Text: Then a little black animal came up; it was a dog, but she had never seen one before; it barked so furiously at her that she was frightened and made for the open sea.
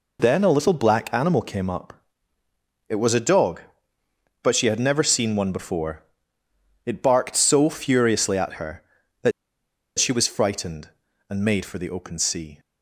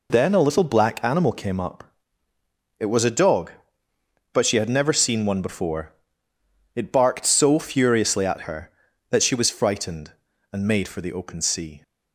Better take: second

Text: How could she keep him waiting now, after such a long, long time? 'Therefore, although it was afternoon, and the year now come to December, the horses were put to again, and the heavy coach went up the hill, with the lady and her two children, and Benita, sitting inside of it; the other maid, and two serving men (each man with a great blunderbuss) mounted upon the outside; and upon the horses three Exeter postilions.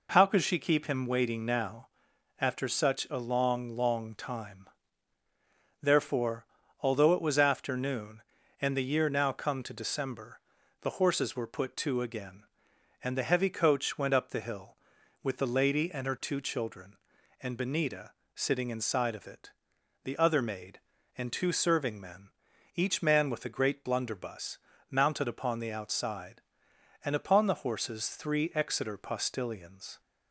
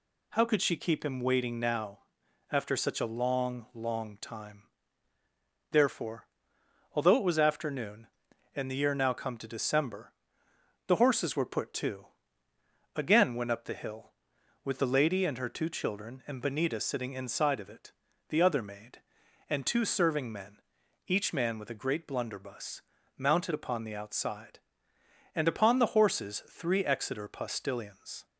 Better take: first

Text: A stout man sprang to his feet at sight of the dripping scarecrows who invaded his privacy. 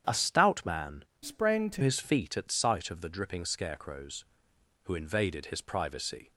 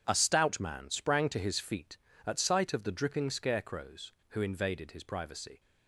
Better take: second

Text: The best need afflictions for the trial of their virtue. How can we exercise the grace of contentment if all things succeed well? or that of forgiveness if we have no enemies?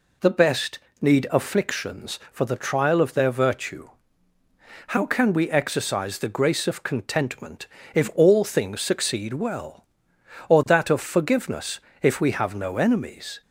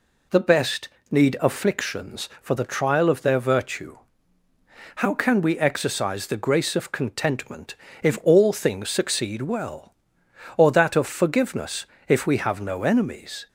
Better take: neither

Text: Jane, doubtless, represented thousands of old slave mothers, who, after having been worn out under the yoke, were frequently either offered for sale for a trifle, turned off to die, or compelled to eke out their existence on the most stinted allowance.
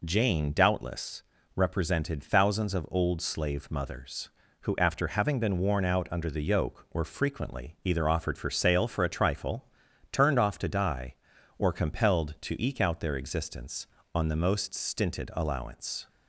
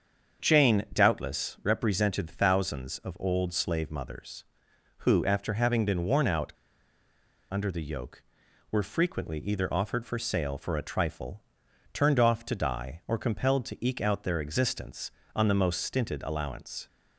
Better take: first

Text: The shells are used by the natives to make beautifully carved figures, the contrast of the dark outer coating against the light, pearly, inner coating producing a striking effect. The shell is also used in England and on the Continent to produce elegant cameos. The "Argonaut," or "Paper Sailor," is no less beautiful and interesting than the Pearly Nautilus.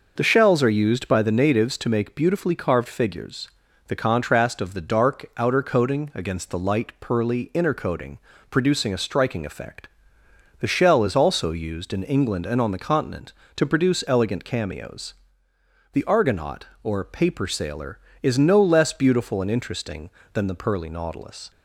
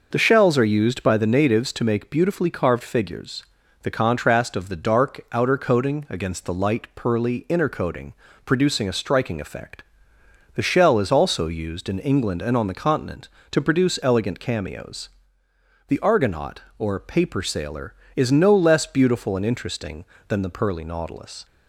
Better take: neither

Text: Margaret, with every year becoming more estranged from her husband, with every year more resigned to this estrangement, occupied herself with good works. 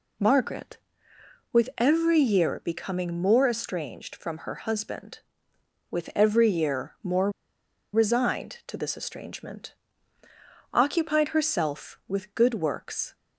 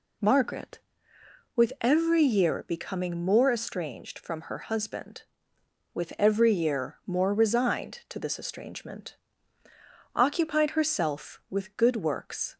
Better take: second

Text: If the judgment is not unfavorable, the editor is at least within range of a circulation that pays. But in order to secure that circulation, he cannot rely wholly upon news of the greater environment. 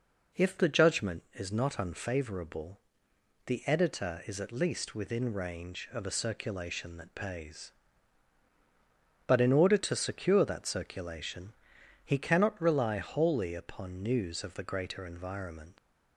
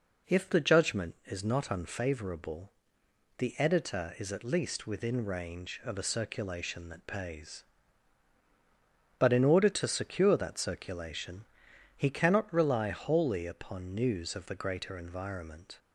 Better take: second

